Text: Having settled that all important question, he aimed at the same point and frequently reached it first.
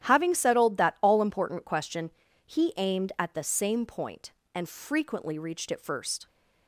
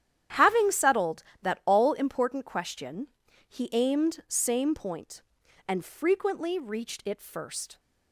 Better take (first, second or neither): first